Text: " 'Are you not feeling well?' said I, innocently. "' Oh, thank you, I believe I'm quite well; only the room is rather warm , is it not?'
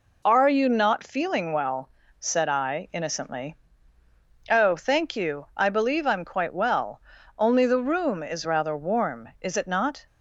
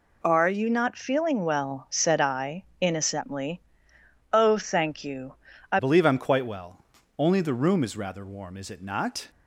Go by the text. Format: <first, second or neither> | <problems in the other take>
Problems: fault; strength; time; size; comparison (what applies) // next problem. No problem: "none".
first | changes voice at "believe"; from 5.7 s on; 3.5 s long